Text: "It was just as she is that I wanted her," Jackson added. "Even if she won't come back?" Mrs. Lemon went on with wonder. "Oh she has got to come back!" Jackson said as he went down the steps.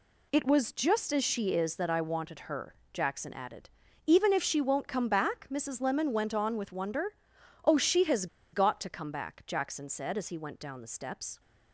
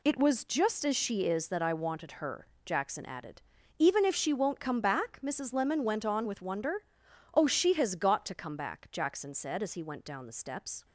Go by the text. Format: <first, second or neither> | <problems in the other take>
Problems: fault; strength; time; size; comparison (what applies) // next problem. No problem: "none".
second | pauses between "has" and "got"; slight; at 8.2 s; 0.27 s long